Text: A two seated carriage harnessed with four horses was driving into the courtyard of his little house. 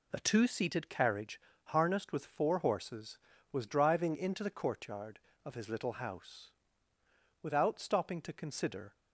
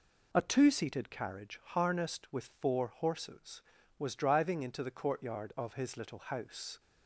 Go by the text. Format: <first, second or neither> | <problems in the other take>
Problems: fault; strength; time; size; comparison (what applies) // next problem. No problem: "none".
second | pauses between "carriage" and "harnessed"; slight; at 1.3 s; 0.26 s long // goes on to say "Without stopping to consider"; from 7.4 s on; 1.5 s long